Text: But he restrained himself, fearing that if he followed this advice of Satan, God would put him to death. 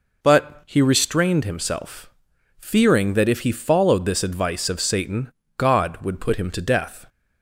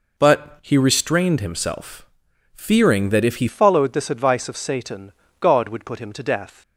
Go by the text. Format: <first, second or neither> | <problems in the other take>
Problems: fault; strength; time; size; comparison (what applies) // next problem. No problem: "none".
first | changes voice at "followed"; from 3.4 s on; 3.2 s long